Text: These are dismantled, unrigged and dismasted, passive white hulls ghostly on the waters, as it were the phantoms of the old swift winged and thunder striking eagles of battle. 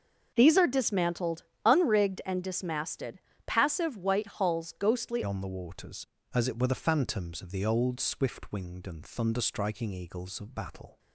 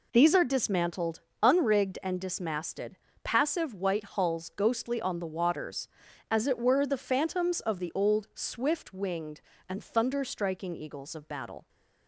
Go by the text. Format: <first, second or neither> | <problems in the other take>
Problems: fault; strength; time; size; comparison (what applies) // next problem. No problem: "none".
second | starts louder than the rest; until 1.3 s; 6 dB // changes voice at "on"; from 5.2 s on; 5.7 s long